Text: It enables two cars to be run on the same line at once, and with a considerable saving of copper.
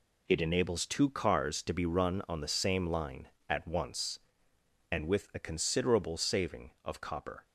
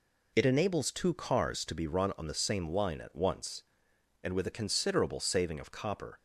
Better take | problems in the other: neither | none

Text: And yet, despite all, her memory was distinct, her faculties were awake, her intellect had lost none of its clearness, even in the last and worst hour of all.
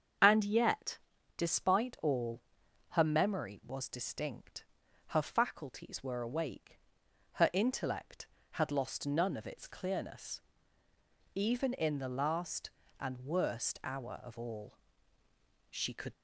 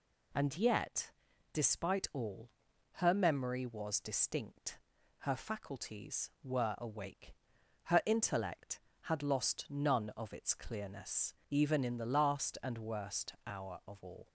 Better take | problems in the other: second | starts louder than the rest; strong; until 1.5 s; 7 dB // goes on to say "She could"; slight; from 15.7 s on; 0.42 s long

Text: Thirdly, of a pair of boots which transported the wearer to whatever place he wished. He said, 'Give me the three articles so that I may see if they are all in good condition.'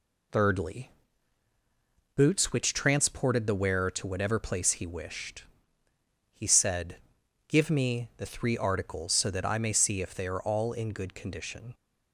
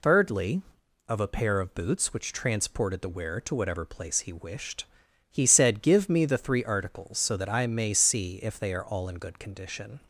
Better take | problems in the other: second | skips "of a pair of"; at 1.5 s

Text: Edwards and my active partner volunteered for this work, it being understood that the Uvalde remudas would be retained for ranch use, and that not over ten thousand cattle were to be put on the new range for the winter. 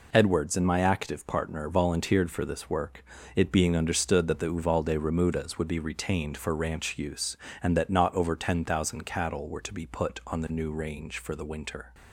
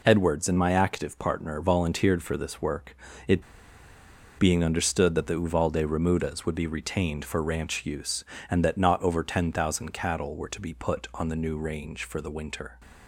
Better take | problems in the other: first | pauses between "it" and "being"; noticeable; at 3.4 s; 0.96 s long

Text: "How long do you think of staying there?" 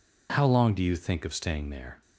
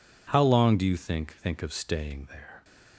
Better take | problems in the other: first | says "think" twice; at 1.3 s

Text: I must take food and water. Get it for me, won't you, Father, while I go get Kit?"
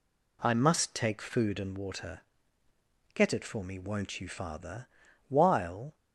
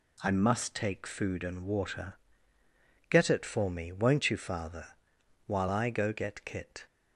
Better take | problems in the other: second | stops before "I go get Kit"; at 5.9 s

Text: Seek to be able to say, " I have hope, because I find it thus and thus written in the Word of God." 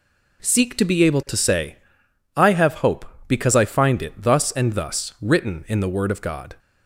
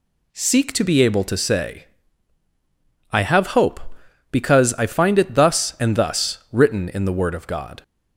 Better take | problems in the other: neither | none

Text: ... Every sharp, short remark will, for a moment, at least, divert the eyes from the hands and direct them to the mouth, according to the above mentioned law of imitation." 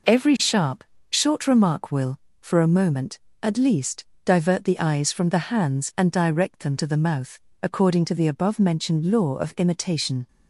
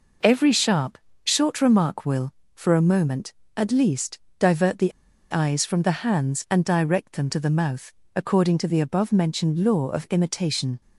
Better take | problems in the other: first | pauses between "the" and "eyes"; at 4.9 s; 0.40 s long

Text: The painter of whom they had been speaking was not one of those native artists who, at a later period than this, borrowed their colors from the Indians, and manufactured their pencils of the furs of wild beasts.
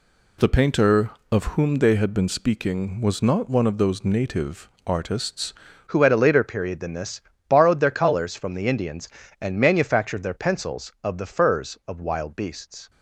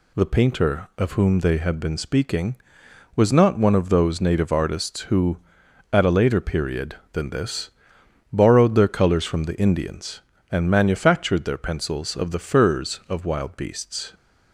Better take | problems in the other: second | pauses between "native" and "artists"; slight; at 4.6 s; 0.16 s long // changes voice at "who"; from 5.8 s on; 7.0 s long

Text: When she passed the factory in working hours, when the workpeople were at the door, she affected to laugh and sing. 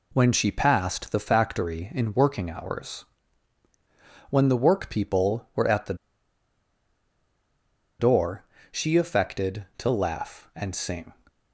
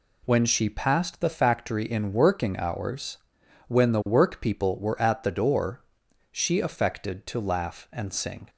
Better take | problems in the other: second | pauses between "the" and "door"; strong; at 5.9 s; 2.0 s long

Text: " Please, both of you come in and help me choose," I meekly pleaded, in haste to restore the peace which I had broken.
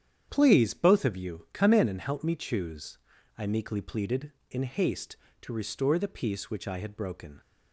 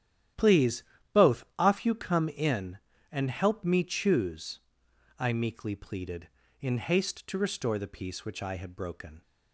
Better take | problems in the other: first | starts louder than the rest; strong; until 1.7 s; 10.5 dB; strong in the first // says "off" for "of"; at 1.5 s

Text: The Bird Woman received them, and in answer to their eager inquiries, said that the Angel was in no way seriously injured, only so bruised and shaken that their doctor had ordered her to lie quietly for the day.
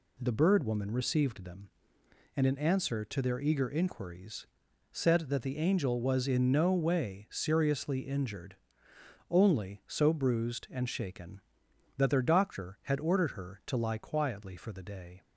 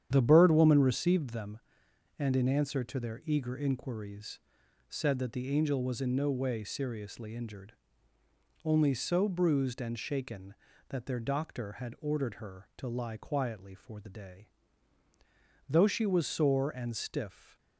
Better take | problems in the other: first | starts louder than the rest; strong; until 1.1 s; 9 dB // goes on to say "Though she was sore and stiff"; strong; from 15.6 s on; 1.8 s long

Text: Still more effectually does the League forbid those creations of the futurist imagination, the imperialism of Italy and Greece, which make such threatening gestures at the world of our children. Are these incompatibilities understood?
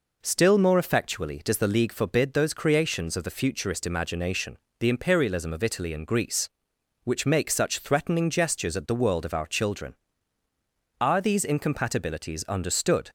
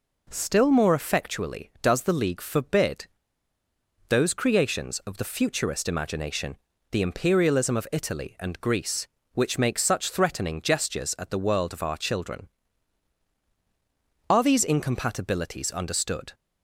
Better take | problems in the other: first | pauses between "forbid" and "those"; at 3.0 s; 1.0 s long

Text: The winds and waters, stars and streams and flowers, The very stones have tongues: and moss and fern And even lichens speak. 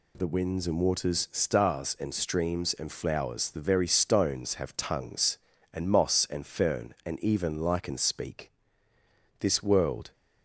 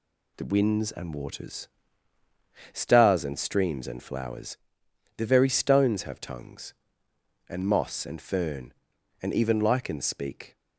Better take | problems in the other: second | goes on to say "This world"; noticeable; from 9.3 s on; 0.72 s long

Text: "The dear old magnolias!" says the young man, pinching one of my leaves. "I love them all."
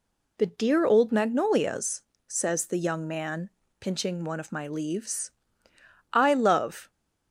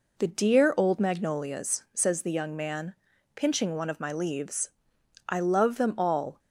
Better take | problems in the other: second | stops before "them all"; at 6.8 s

